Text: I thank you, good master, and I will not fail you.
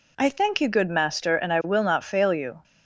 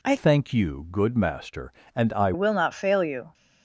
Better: first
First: none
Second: changes voice from "thank" to "I"; from 0.1 to 2.3 s; 2.2 s long

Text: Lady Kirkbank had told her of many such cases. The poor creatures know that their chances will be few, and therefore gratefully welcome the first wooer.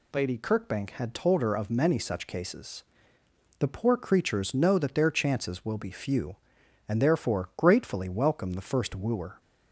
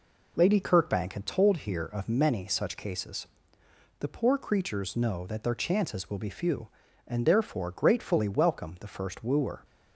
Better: first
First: none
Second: says "here" for "her"; at 1.5 s

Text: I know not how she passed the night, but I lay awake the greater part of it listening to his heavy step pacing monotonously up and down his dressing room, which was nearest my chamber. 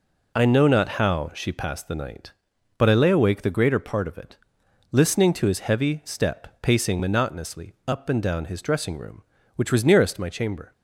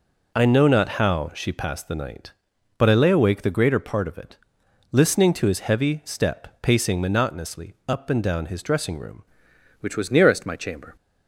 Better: first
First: pauses between "it" and "listening"; noticeable; at 4.3 s; 0.54 s long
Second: pauses between "it" and "listening"; noticeable; at 4.3 s; 0.54 s long // changes voice at "which"; from 9.7 s on; 1.2 s long

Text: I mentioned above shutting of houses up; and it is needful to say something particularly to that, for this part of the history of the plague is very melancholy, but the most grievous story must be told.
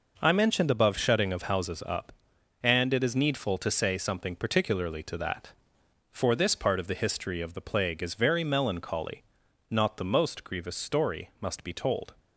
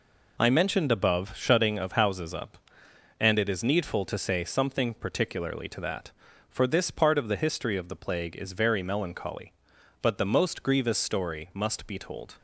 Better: second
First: says "not" for "but"; at 9.6 s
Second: none

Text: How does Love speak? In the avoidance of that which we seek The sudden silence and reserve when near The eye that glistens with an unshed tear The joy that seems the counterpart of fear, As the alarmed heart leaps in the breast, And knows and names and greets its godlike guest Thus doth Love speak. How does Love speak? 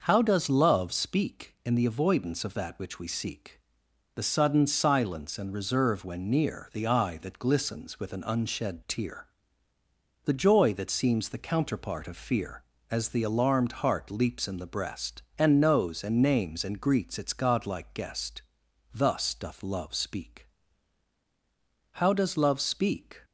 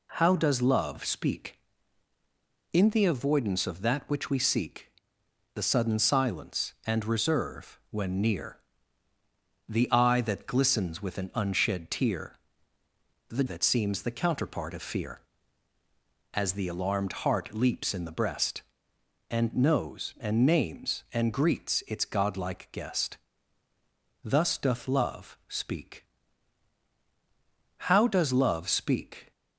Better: first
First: pauses between "seek" and "The"; noticeable; at 3.5 s; 0.56 s long // pauses between "tear" and "The"; noticeable; at 9.2 s; 0.97 s long // pauses between "guest" and "Thus"; noticeable; at 18.4 s; 0.54 s long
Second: pauses between "seek" and "The"; noticeable; at 4.9 s; 0.64 s long // pauses between "near" and "The"; at 8.5 s; 1.0 s long // pauses between "tear" and "The"; noticeable; at 12.3 s; 0.94 s long // skips "joy"; at 13.4 s // pauses between "guest" and "Thus"; at 23.1 s; 1.0 s long

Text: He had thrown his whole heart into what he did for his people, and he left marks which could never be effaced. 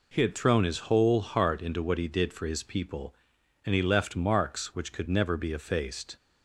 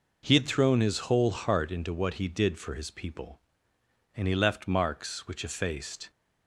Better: first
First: none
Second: skips "could never be"; at 5.4 s

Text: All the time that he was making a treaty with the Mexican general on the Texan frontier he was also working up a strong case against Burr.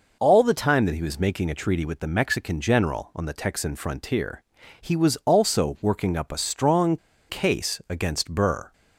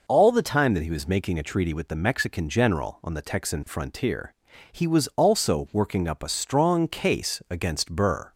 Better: second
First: pauses between "frontier" and "he"; at 4.4 s; 0.38 s long // pauses between "strong" and "case"; slight; at 6.9 s; 0.33 s long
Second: pauses between "frontier" and "he"; at 4.3 s; 0.38 s long

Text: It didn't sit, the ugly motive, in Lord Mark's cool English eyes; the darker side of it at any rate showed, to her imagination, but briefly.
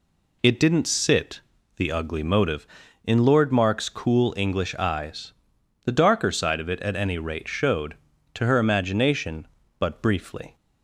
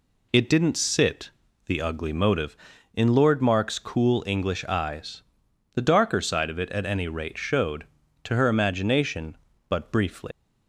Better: first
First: none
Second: leaves "briefly" unfinished; at 10.3 s; 135 ms

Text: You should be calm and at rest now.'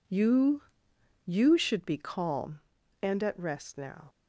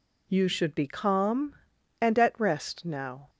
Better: second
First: says "You" twice; at 1.2 s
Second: none

